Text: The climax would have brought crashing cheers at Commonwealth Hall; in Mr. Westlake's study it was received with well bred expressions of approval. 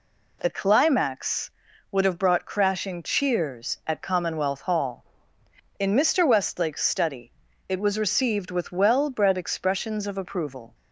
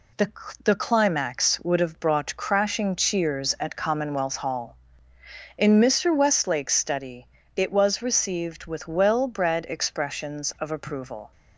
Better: first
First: pauses between "study" and "it"; slight; at 7.3 s; 0.36 s long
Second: says "The" twice; at 0.6 s // pauses between "study" and "it"; slight; at 7.2 s; 0.30 s long

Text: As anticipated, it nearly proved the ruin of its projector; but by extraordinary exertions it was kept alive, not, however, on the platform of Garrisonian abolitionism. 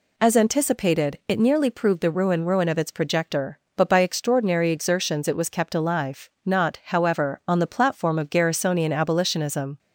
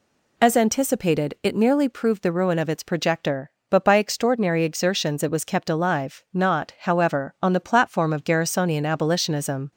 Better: second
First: says "ruin" twice; at 2.4 s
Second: none

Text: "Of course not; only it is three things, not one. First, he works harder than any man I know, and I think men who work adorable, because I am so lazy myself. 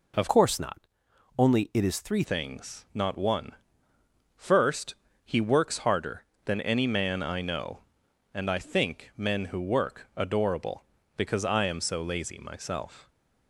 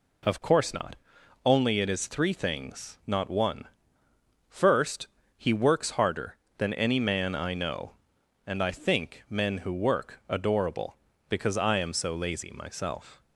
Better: second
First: changes voice from "course" to "three"; from 0.2 to 2.2 s; 2.0 s long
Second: none

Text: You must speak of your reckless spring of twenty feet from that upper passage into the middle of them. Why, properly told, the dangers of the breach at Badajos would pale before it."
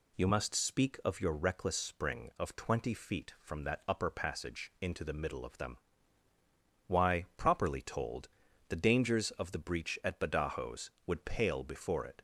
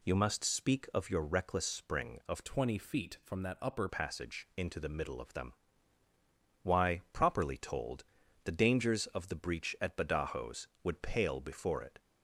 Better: first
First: none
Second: changes voice from "twenty" to "upper"; from 2.4 to 3.8 s; 1.4 s long

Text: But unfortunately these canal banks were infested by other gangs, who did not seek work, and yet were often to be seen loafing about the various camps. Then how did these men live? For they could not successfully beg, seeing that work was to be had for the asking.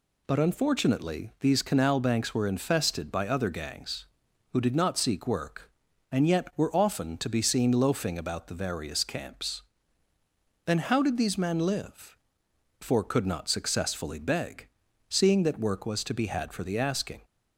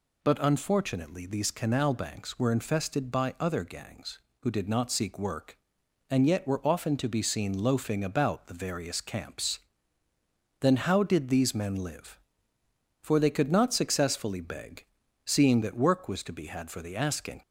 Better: second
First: skips "they"; at 13.0 s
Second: none

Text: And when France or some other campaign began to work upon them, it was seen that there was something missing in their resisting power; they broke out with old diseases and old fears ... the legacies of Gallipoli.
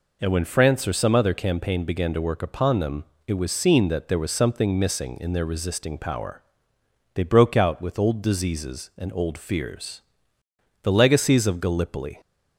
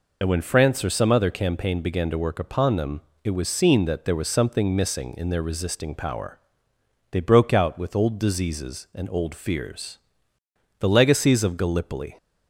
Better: first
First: none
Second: loses the start of "And"; at 0.2 s; 30 ms

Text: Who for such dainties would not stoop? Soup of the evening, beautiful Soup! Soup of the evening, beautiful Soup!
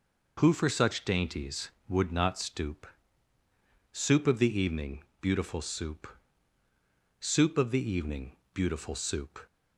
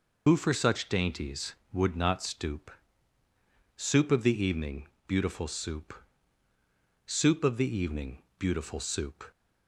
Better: first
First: none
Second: loses the start of "Who"; at 0.2 s; 55 ms

